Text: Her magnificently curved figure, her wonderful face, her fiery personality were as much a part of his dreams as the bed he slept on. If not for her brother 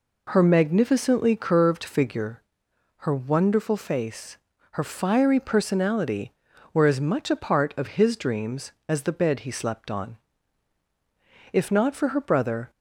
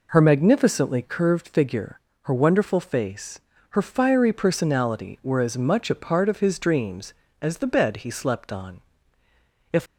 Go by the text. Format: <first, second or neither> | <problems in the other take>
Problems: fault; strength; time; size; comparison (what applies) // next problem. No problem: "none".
first | stops before "not for her brother"; at 9.8 s